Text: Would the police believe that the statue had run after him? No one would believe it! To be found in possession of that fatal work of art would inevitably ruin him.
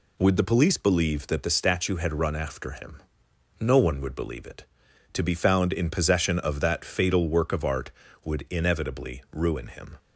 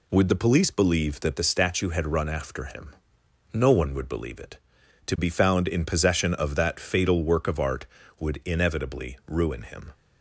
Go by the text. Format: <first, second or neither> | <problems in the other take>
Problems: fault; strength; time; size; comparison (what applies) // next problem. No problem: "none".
neither | none